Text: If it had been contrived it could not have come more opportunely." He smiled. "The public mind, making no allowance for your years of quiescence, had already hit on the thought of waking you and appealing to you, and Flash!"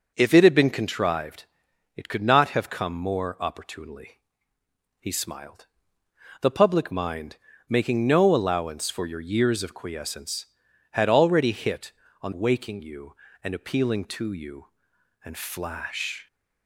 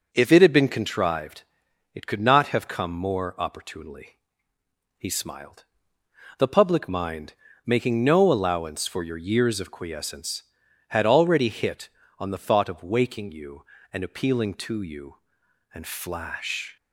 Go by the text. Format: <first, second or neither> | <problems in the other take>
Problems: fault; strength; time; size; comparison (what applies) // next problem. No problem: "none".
second | pauses between "contrived" and "it"; noticeable; at 1.4 s; 0.50 s long; noticeable in the second // skips "the thought of"; at 12.3 s